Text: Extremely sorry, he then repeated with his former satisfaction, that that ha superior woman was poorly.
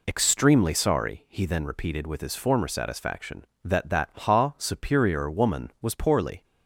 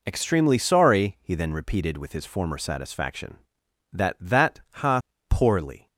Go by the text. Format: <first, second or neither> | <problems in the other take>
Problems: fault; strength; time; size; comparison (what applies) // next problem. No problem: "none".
first | skips "superior woman was"; at 5.1 s